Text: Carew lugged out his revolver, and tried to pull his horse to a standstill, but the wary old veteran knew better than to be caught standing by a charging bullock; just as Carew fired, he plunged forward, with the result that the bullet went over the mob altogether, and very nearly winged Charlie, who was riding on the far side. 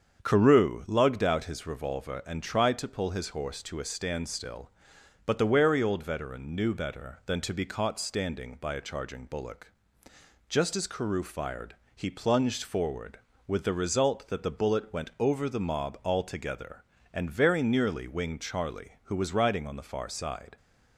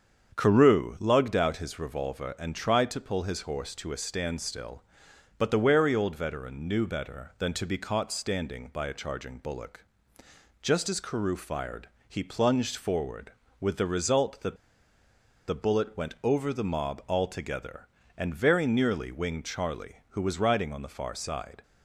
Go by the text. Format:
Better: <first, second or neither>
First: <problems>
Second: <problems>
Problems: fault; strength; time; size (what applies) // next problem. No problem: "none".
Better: first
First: starts louder than the rest; strong; until 1.2 s; 7.5 dB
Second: starts louder than the rest; strong; until 1.4 s; 7.5 dB // pauses between "that" and "the"; noticeable; at 14.5 s; 0.92 s long